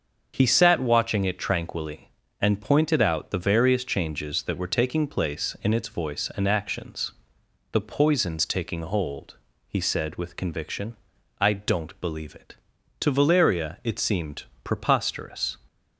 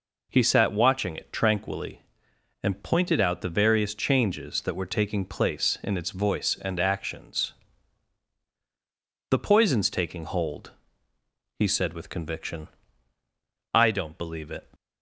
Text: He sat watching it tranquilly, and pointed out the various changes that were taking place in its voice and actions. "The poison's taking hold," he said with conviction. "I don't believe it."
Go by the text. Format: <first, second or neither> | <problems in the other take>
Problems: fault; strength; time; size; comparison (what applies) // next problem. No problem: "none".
second | starts louder than the rest; until 1.4 s; 7 dB // goes on to say "To Valeria it seemed preposterous"; strong; from 12.9 s on; 2.5 s long